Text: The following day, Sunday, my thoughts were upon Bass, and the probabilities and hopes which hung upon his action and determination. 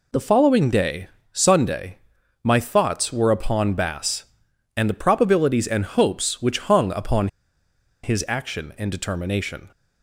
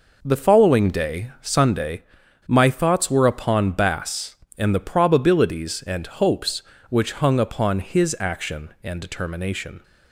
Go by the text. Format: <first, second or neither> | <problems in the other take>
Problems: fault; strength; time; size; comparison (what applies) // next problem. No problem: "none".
second | pauses between "upon" and "his"; noticeable; at 7.2 s; 0.76 s long